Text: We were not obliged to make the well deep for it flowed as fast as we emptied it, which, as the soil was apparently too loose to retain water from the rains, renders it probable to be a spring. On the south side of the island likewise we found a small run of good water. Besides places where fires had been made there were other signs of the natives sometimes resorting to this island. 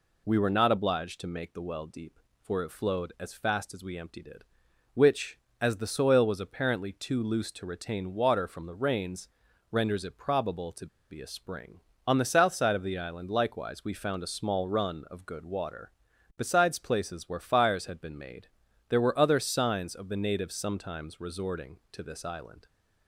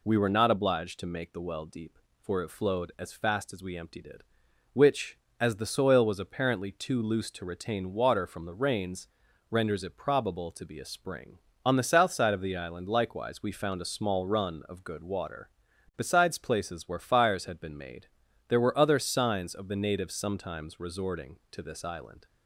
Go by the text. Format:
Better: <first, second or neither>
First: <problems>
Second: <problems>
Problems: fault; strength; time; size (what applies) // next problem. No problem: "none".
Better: second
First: pauses between "to" and "be"; slight; at 10.8 s; 0.24 s long // pauses between "made" and "there"; at 18.4 s; 0.42 s long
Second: pauses between "made" and "there"; at 18.0 s; 0.42 s long